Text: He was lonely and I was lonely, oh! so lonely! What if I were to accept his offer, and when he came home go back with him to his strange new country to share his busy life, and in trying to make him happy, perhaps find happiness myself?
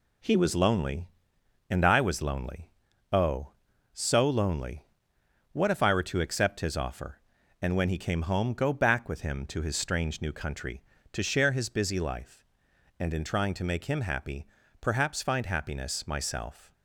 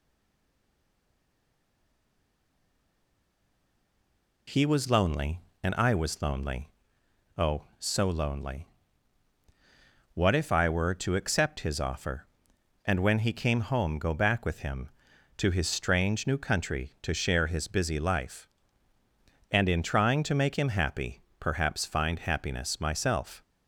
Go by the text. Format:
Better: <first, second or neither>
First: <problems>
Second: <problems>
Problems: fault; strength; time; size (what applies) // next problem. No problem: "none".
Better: first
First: none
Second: stays silent before the first word; strong; until 4.4 s; 4.4 s long